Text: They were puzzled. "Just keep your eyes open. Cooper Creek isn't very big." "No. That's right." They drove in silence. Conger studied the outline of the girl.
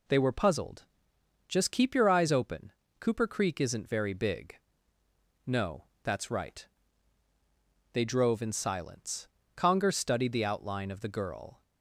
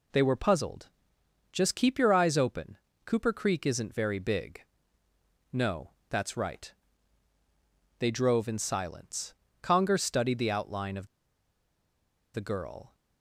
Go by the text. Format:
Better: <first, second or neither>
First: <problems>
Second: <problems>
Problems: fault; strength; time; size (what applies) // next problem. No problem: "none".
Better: first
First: none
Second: pauses between "of" and "the"; strong; at 11.0 s; 1.2 s long